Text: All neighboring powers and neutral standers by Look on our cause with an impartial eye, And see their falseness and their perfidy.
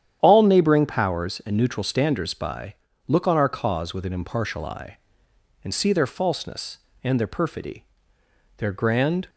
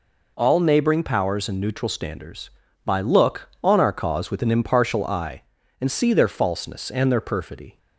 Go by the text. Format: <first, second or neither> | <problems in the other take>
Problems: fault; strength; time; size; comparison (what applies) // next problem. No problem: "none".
second | starts louder than the rest; strong; until 1.2 s; 9.5 dB // pauses between "by" and "Look"; slight; at 2.7 s; 0.32 s long // goes on to say "Their grand"; noticeable; from 8.5 s on; 0.70 s long